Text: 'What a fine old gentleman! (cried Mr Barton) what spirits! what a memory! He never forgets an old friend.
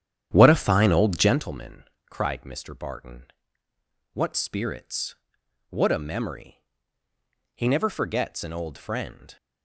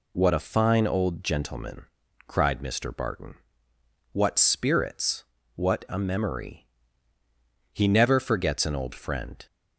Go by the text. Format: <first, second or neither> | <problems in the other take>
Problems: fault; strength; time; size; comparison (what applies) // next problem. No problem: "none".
second | starts louder than the rest; strong; until 1.5 s; 10 dB